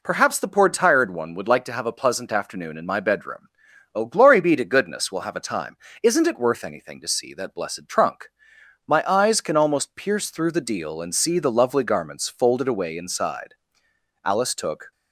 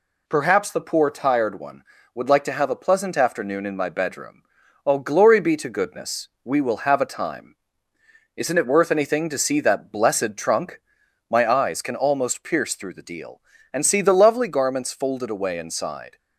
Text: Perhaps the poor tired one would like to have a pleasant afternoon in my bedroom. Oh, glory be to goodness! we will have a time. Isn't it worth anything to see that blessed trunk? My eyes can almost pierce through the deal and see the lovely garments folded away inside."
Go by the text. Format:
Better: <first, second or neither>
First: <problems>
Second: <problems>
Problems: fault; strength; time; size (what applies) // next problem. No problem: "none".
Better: second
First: goes on to say "Alice took"; noticeable; from 14.2 s on; 0.66 s long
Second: none